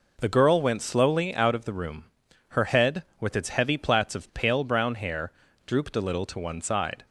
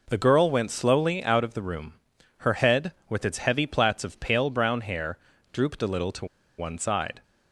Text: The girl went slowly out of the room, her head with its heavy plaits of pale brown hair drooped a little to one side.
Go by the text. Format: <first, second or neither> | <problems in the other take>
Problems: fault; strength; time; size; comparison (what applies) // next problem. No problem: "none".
first | pauses between "hair" and "drooped"; slight; at 5.1 s; 0.34 s long; slight in the first // pauses between "to" and "one"; slight; at 6.2 s; 0.32 s long